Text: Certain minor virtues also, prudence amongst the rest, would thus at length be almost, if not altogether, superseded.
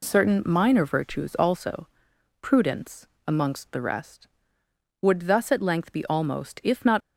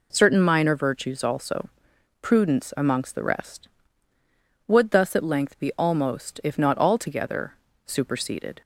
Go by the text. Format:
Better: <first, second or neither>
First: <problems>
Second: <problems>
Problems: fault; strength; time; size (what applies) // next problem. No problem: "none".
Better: second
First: pauses between "prudence" and "amongst"; slight; at 3.0 s; 0.18 s long // stops before "altogether superseded"; at 7.0 s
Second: none